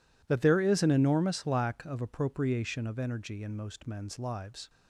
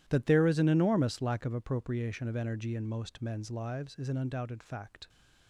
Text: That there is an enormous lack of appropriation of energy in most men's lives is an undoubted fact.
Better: second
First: stops before "is an undoubted fact"; at 4.6 s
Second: none

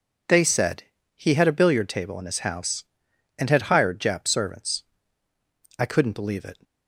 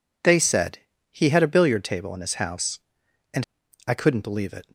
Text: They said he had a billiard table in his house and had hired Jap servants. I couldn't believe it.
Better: first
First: pauses between "said" and "he"; slight; at 0.8 s; 0.30 s long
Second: pauses between "said" and "he"; slight; at 0.7 s; 0.30 s long // skips "had hired Jap servants"; at 3.6 s

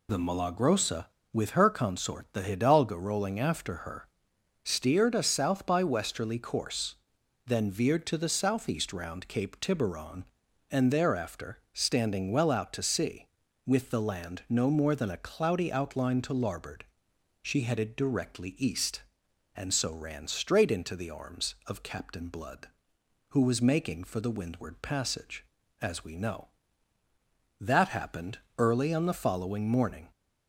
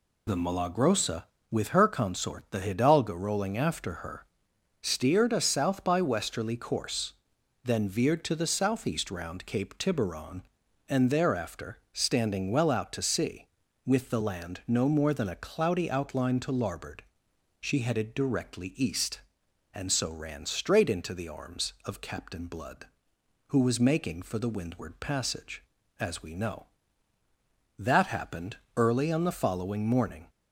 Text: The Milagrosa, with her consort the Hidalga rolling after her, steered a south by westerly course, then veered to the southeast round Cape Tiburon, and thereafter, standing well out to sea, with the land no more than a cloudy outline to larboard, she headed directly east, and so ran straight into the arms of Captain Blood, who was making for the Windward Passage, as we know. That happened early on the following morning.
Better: neither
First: pauses between "happened" and "early"; slight; at 28.3 s; 0.18 s long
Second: pauses between "happened" and "early"; slight; at 28.5 s; 0.18 s long

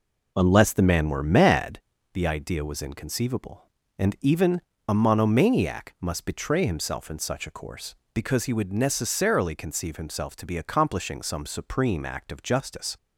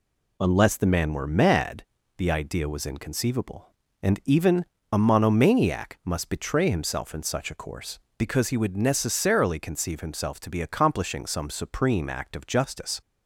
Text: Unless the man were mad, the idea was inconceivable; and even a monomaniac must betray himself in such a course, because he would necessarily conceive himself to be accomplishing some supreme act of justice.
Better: second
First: starts louder than the rest; noticeable; until 1.9 s; 4.5 dB // pauses between "even" and "a"; slight; at 4.6 s; 0.26 s long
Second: pauses between "even" and "a"; slight; at 4.6 s; 0.26 s long

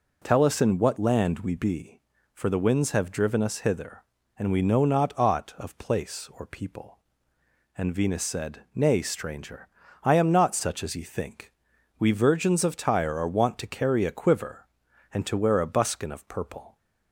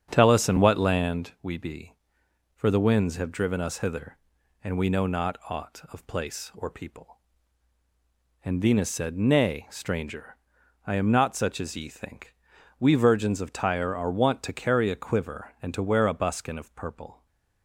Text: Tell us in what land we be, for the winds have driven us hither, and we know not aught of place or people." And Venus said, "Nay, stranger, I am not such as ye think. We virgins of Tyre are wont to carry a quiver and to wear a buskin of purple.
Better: first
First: none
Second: starts louder than the rest; strong; until 1.3 s; 7.5 dB // stays silent after the last word; slight; from 17.1 s on; 0.5 s long

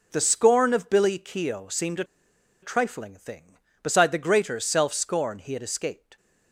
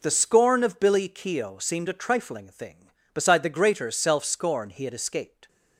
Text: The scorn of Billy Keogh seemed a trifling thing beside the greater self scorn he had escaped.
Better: second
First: pauses between "a" and "trifling"; noticeable; at 2.0 s; 0.57 s long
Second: none

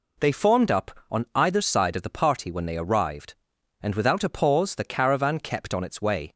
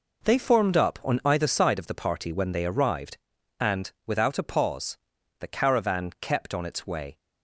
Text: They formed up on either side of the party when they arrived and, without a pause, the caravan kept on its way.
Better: first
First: none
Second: gets quieter; strong; throughout; 9.5 dB

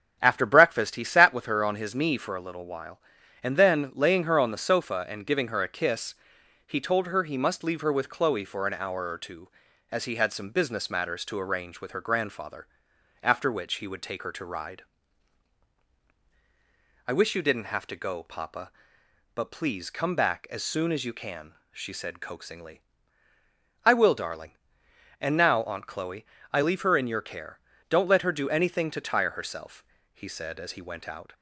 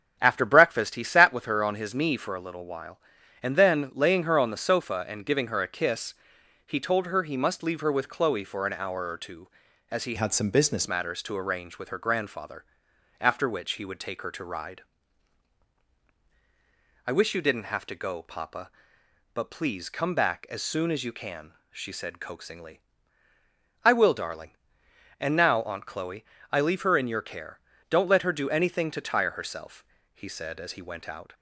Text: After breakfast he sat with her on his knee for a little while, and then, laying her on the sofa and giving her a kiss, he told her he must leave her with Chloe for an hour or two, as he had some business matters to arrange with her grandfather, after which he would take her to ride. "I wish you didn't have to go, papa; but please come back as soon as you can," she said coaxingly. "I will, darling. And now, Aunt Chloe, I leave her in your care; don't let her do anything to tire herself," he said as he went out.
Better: first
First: starts louder than the rest; strong; until 1.2 s; 7.5 dB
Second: starts louder than the rest; strong; until 1.2 s; 8 dB // changes voice from "had" to "business"; from 10.1 to 10.8 s; 0.7 s long

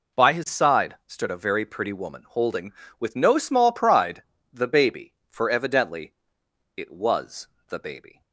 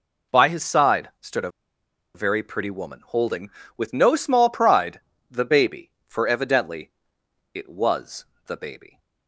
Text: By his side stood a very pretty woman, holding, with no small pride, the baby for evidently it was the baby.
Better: first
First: pauses between "evidently" and "it"; noticeable; at 6.1 s; 0.64 s long // pauses between "was" and "the"; slight; at 7.4 s; 0.18 s long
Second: pauses between "a" and "very"; noticeable; at 1.5 s; 0.63 s long // pauses between "evidently" and "it"; noticeable; at 6.9 s; 0.64 s long // pauses between "was" and "the"; slight; at 8.2 s; 0.18 s long

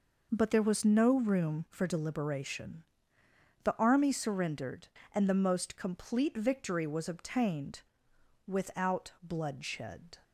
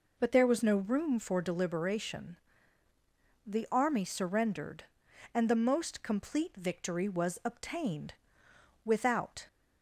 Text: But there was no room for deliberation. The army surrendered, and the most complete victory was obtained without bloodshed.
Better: first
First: pauses between "obtained" and "without"; noticeable; at 7.8 s; 0.66 s long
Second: pauses between "obtained" and "without"; noticeable; at 8.1 s; 0.70 s long // stops before "bloodshed"; at 9.4 s

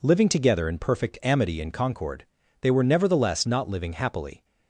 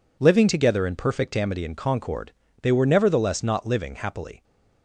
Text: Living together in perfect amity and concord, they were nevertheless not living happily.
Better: neither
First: none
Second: none

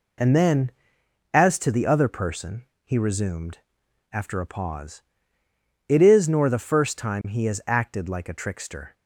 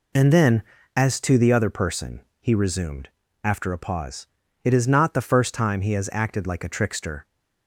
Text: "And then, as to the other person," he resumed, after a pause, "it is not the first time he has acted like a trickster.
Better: second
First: says "nor" for "not"; at 6.2 s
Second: none

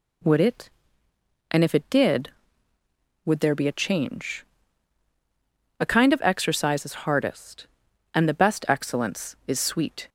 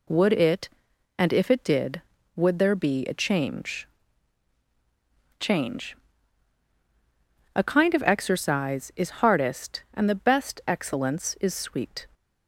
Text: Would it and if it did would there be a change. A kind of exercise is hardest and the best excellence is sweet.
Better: first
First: none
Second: says "change" twice; at 5.3 s

